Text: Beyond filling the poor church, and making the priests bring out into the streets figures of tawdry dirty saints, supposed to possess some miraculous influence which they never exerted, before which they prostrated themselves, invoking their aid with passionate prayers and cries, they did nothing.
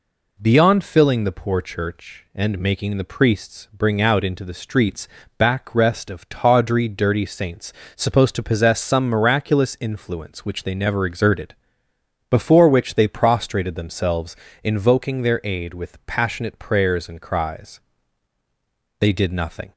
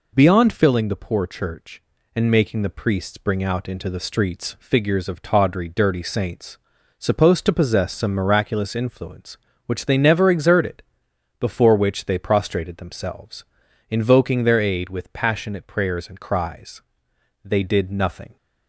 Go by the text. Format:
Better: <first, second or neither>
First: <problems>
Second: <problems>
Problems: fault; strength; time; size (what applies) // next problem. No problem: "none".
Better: second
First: says "backrest" for "figures"; at 5.3 s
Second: none